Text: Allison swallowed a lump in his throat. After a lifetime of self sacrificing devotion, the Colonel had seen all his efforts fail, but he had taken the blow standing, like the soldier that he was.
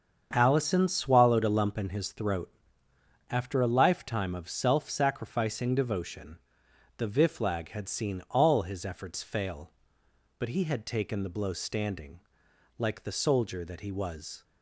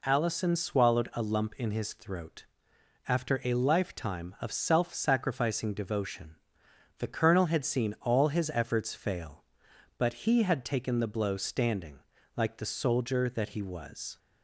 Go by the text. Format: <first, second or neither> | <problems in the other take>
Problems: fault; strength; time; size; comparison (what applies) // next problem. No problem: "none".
second | starts louder than the rest; strong; until 1.3 s; 7 dB // says "Viflag" for "Colonel"; at 7.0 s